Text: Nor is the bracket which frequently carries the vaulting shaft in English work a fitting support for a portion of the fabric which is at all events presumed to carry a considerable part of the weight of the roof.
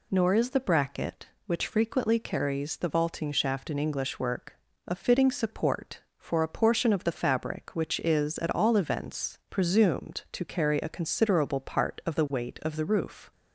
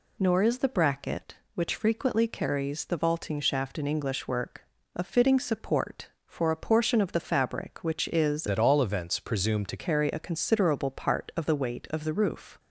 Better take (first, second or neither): first